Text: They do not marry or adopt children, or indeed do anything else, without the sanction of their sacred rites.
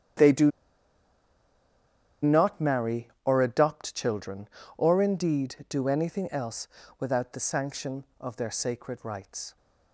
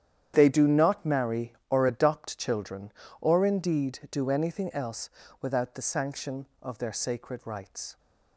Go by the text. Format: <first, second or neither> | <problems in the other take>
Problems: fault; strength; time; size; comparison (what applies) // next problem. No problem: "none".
second | starts louder than the rest; strong; until 2.9 s; 9.5 dB; strong in the second // pauses between "do" and "not"; strong; at 0.5 s; 1.7 s long